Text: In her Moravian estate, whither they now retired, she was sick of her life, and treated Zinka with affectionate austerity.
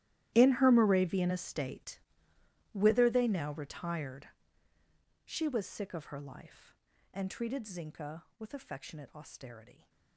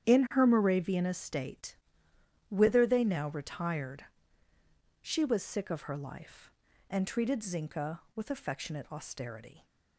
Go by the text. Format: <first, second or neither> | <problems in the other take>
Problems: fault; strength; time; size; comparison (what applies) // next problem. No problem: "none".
second | gets quieter; strong; throughout; 18 dB // starts louder than the rest; strong; until 1.3 s; 13.5 dB; strong in the second